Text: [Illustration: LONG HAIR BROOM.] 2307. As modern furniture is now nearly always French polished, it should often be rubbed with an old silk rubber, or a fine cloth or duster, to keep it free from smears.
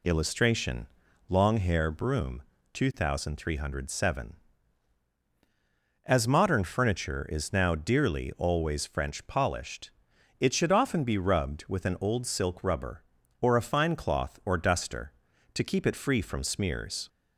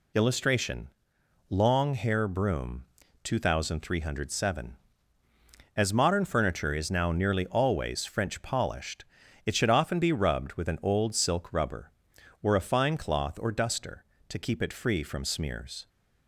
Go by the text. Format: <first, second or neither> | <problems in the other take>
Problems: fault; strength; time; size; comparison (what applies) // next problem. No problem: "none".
second | says "dearly" for "nearly"; at 7.7 s